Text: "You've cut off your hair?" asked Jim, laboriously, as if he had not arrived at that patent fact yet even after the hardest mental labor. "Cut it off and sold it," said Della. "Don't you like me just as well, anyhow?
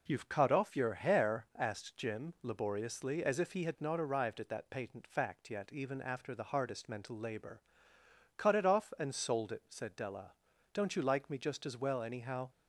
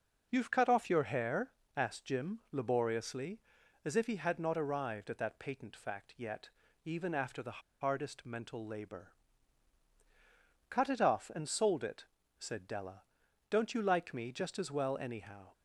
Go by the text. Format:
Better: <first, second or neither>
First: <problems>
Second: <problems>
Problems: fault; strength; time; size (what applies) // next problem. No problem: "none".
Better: first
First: none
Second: pauses between "yet" and "even"; slight; at 6.4 s; 0.36 s long // pauses between "the" and "hardest"; slight; at 7.5 s; 0.22 s long